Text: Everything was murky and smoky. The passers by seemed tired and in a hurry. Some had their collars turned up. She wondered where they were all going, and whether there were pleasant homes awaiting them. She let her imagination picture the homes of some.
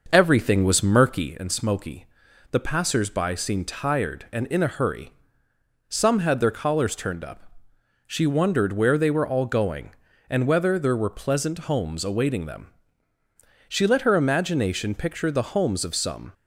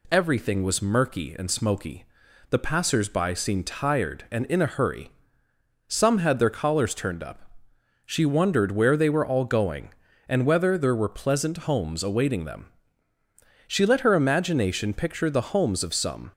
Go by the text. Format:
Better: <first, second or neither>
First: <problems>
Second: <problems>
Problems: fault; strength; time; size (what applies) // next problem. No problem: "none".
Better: second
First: starts louder than the rest; noticeable; until 1.4 s; 6 dB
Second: none